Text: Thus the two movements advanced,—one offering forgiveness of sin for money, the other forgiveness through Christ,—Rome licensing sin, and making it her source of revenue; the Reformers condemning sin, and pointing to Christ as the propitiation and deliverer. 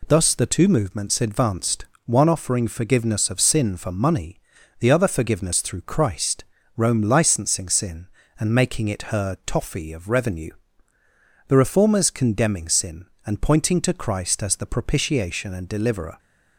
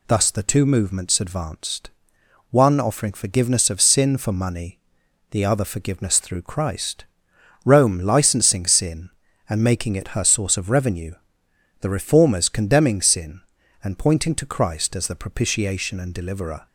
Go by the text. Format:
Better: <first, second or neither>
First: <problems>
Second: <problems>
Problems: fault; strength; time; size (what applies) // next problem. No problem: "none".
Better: second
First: says "toffee" for "source"; at 9.4 s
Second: none